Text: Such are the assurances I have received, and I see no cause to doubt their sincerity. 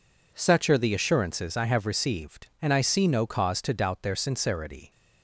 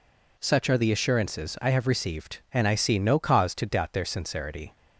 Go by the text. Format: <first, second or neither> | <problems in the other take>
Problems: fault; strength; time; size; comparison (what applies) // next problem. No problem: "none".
neither | none